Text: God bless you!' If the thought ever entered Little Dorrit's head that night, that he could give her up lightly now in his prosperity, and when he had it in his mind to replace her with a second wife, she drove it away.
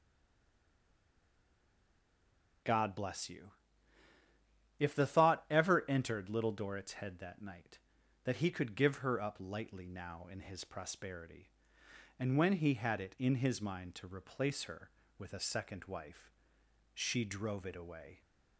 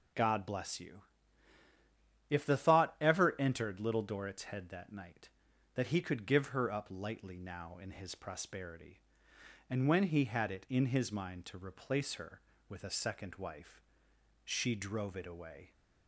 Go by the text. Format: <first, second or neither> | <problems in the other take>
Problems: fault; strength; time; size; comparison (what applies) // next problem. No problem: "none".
second | stays silent before the first word; strong; until 2.6 s; 2.6 s long